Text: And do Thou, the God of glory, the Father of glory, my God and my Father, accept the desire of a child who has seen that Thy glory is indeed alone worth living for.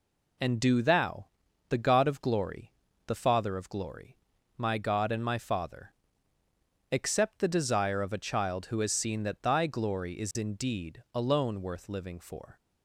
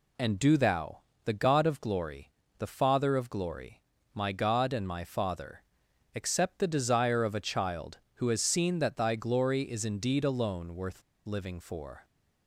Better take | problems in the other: first | pauses between "worth" and "living"; slight; at 11.0 s; 0.24 s long

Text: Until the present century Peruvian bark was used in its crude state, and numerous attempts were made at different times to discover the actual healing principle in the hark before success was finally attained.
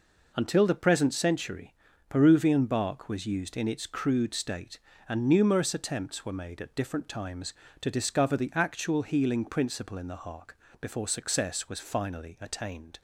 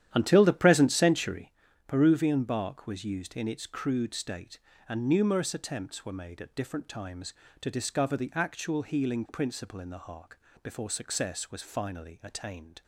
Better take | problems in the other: first | starts louder than the rest; strong; until 1.5 s; 11 dB // pauses between "century" and "Peruvian"; slight; at 1.5 s; 0.34 s long; slight in the first // pauses between "hark" and "before"; slight; at 10.3 s; 0.22 s long; slight in the first

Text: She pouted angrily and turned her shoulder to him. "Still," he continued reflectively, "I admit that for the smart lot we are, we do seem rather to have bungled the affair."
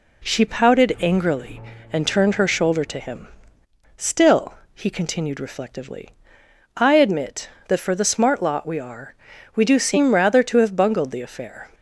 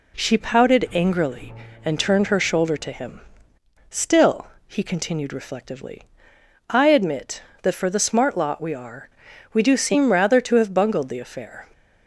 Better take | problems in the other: neither | none

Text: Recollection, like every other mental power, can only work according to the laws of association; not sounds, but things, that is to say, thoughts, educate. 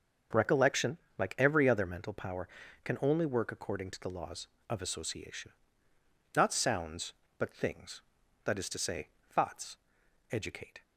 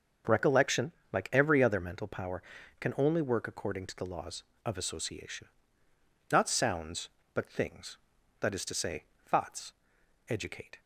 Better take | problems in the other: neither | starts louder than the rest; the same in both

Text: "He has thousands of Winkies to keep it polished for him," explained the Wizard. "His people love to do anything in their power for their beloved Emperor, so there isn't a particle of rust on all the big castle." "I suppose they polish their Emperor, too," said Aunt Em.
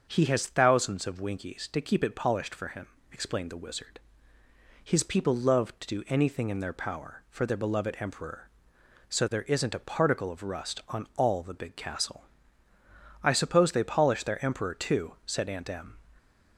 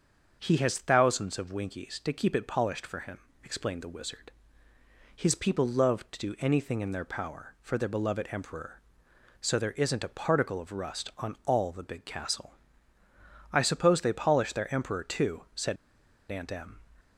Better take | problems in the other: first | starts louder than the rest; until 1.4 s; 7 dB; also in the first // pauses between "said" and "Aunt"; noticeable; at 15.7 s; 0.54 s long

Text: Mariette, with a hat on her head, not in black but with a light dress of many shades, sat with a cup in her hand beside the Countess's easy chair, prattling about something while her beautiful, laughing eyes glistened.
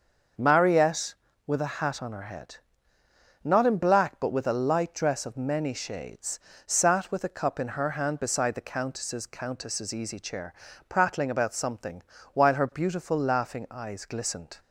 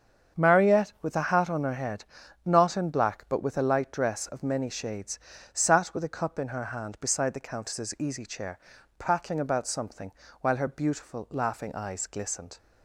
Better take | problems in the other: second | starts louder than the rest; until 1.7 s; 6.5 dB; strong in the second // says "Countess's" twice; at 9.2 s // pauses between "something" and "while"; slight; at 12.0 s; 0.32 s long; slight in the second

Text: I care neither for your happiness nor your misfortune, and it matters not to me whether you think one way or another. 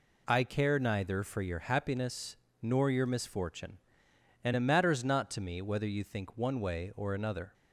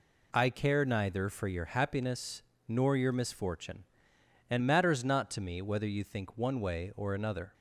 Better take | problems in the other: first | pauses between "happiness" and "nor"; slight; at 2.4 s; 0.26 s long; slight in the first // skips "it"; at 4.6 s

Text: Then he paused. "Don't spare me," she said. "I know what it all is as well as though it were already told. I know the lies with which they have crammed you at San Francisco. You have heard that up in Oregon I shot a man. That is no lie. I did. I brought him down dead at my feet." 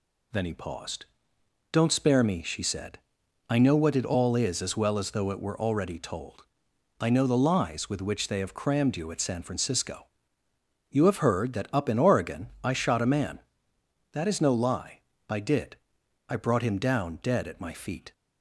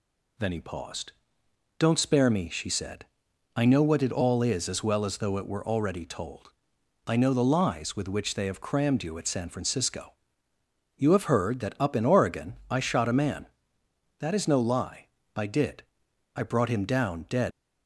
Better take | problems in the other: first | stops before "at my feet"; at 17.5 s

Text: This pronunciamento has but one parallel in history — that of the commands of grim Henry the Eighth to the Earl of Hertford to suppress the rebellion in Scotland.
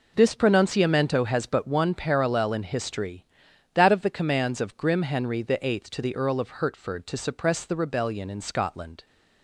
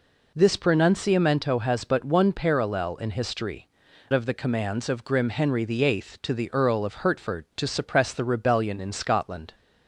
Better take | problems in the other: first | skips "that"; at 3.8 s

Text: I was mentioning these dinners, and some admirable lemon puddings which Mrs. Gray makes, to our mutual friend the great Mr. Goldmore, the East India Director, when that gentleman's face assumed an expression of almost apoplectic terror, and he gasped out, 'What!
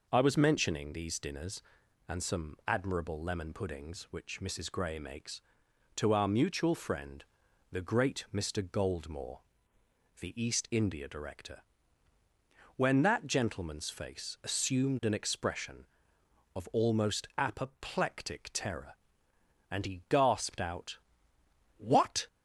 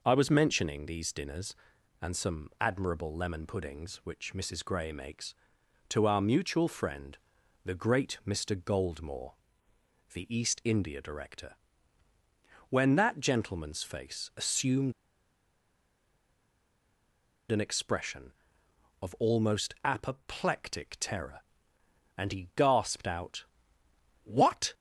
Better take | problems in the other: first | pauses between "friend" and "the"; at 7.1 s; 0.44 s long; also in the first // pauses between "assumed" and "an"; strong; at 14.9 s; 2.5 s long

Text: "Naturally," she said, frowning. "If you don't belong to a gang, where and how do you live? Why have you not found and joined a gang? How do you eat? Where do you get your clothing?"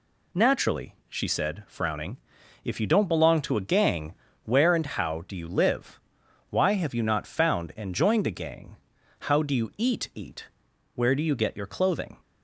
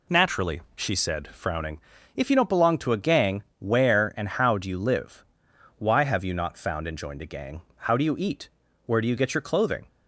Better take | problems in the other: second | says "eat" twice; at 10.1 s

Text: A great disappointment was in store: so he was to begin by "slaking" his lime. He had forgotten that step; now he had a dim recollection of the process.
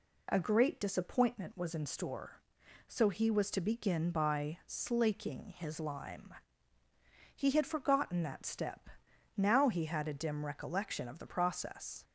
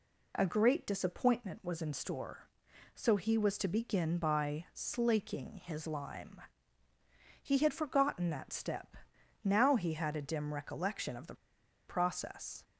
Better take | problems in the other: first | pauses between "the" and "process"; noticeable; at 11.3 s; 0.54 s long

